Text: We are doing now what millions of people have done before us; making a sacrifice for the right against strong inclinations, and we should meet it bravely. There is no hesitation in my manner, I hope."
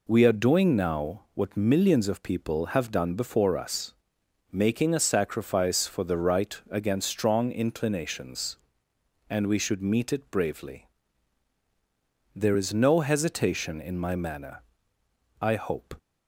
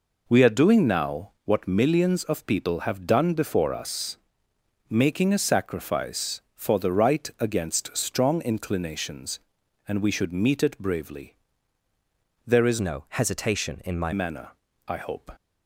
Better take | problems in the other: first | changes voice from "no" to "my"; from 12.7 to 14.1 s; 1.4 s long

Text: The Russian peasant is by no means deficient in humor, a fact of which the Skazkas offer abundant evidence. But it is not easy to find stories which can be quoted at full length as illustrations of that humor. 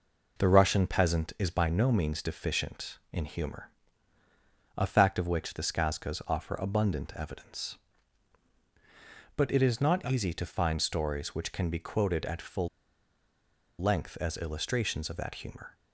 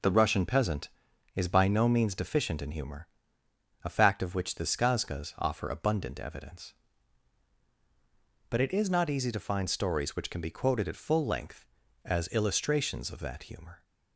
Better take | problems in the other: second | pauses between "full" and "length"; at 12.6 s; 1.1 s long

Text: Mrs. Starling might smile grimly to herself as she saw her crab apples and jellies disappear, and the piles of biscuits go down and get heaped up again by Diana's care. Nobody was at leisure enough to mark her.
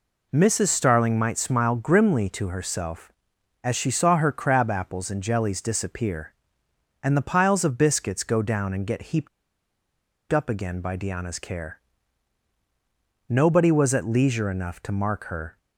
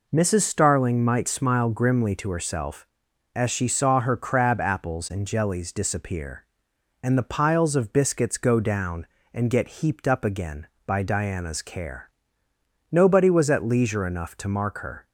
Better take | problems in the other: second | pauses between "heaped" and "up"; at 9.2 s; 1.0 s long

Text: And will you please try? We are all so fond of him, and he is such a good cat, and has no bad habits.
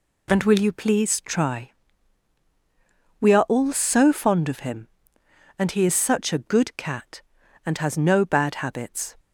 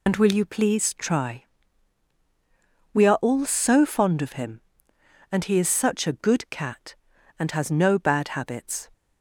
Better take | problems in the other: first | loses the start of "And"; at 0.0 s; 50 ms

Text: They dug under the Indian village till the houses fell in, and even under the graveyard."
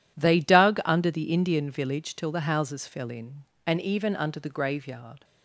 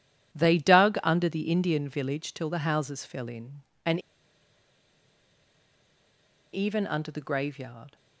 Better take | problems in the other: first | pauses between "and" and "even"; strong; at 3.9 s; 2.5 s long

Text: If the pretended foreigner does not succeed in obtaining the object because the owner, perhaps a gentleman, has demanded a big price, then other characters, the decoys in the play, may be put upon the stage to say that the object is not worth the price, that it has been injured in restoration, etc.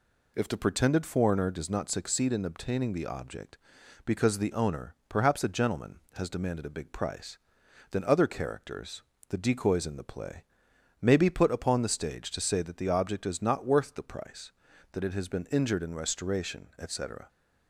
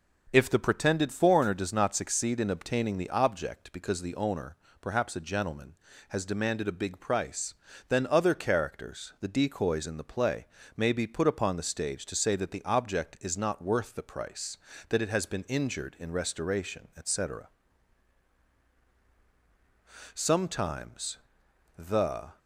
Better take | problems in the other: first | starts louder than the rest; noticeable; until 1.3 s; 6 dB // goes on to say "Sometimes the"; strong; from 20.1 s on; 2.2 s long

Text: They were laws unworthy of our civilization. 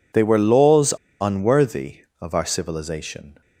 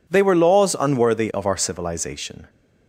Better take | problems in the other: second | pauses between "laws" and "unworthy"; slight; at 0.9 s; 0.26 s long

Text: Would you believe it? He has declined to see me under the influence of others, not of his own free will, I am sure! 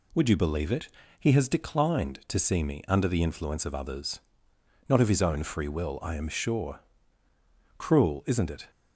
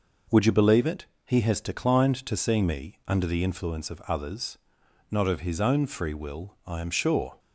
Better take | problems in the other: second | goes on to say "Cruel isn't it"; noticeable; from 7.7 s on; 0.92 s long

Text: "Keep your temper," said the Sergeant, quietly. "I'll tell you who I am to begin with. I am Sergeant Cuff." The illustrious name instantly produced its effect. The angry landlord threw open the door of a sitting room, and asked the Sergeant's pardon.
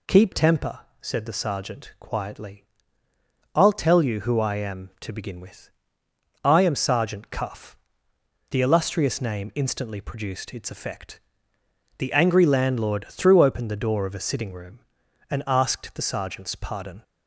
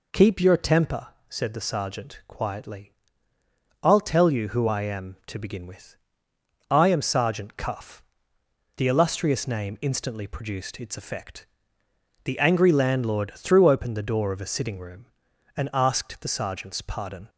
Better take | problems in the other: second | skips "your"; at 0.3 s

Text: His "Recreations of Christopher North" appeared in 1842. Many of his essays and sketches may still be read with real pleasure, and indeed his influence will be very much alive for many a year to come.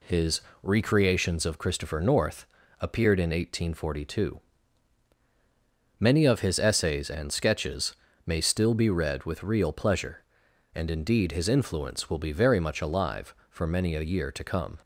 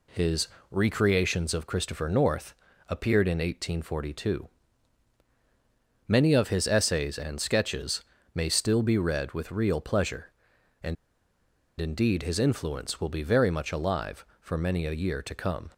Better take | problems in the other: first | pauses between "His" and "Recreations"; slight; at 0.4 s; 0.24 s long; slight in the first // pauses between "North" and "appeared"; slight; at 2.5 s; 0.32 s long; slight in the first // pauses between "sketches" and "may"; slight; at 8.0 s; 0.32 s long; slight in the first // pauses between "and" and "indeed"; noticeable; at 10.9 s; 0.84 s long

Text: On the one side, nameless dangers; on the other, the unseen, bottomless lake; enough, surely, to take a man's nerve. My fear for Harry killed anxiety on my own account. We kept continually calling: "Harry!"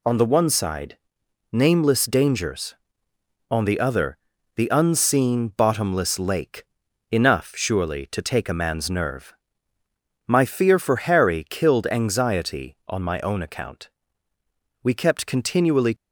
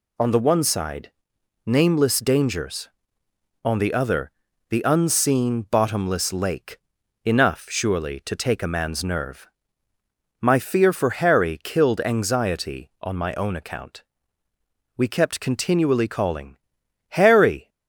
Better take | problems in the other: second | stops before "calling Harry"; at 15.9 s

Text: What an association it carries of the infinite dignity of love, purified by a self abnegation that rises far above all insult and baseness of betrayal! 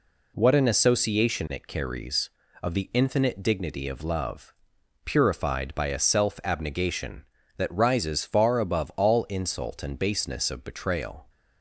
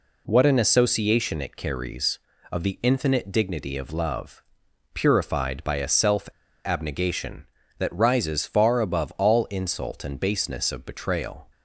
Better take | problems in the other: first | pauses between "self" and "abnegation"; at 6.2 s; 0.36 s long

